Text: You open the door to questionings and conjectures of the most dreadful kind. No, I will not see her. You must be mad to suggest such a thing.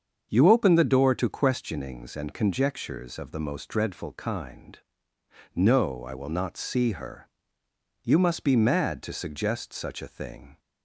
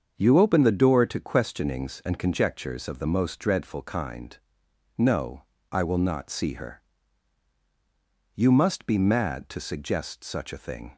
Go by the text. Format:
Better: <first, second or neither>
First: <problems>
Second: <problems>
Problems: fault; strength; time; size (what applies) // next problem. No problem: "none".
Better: neither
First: starts louder than the rest; until 1.3 s; 7 dB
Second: starts louder than the rest; until 1.1 s; 7 dB